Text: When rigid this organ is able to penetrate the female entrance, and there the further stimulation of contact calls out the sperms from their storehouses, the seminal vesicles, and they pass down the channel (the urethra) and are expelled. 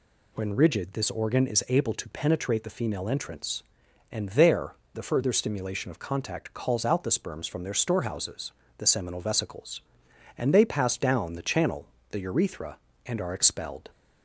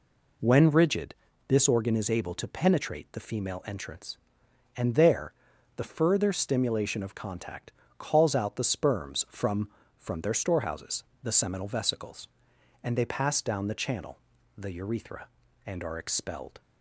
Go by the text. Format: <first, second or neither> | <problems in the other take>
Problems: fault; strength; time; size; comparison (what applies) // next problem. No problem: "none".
first | pauses between "rigid" and "this"; slight; at 1.1 s; 0.36 s long // pauses between "there" and "the"; at 5.3 s; 0.44 s long; slight in the first // pauses between "contact" and "calls"; slight; at 7.7 s; 0.28 s long // says "from" twice; at 9.9 s